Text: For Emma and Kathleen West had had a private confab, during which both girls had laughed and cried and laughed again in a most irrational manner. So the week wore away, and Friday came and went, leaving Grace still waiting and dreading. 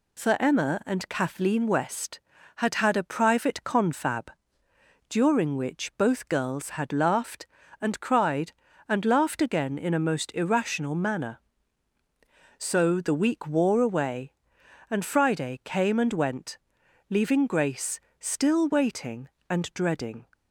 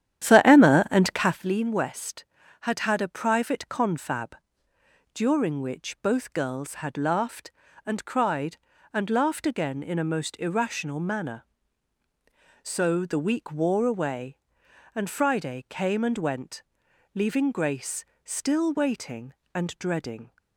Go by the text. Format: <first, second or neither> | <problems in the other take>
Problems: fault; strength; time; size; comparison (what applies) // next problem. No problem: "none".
first | starts louder than the rest; strong; until 1.5 s; 10.5 dB // pauses between "Grace" and "still"; slight; at 18.0 s; 0.18 s long; slight in the first